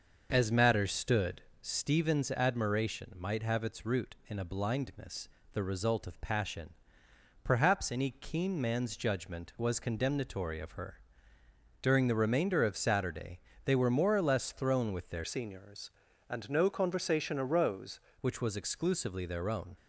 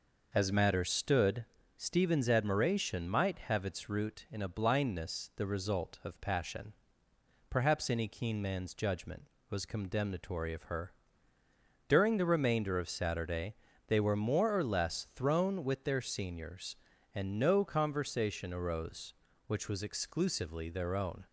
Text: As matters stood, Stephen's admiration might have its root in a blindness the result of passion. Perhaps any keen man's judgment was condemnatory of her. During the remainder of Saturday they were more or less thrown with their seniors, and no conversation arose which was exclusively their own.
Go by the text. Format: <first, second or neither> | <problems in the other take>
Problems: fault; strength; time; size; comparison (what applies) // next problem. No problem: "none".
second | starts louder than the rest; noticeable; until 1.3 s; 6 dB // pauses between "blindness" and "the"; slight; at 5.2 s; 0.24 s long // pauses between "Saturday" and "they"; slight; at 13.4 s; 0.24 s long; slight in the second // changes voice from "seniors" to "arose"; from 15.2 to 17.9 s; 2.7 s long